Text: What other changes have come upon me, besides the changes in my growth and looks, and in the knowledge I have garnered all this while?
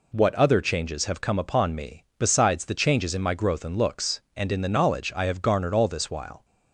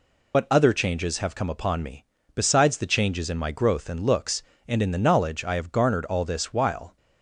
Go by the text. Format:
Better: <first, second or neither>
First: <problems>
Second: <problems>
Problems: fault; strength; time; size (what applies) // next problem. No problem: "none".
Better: first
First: none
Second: loses the start of "What"; at 0.3 s; 85 ms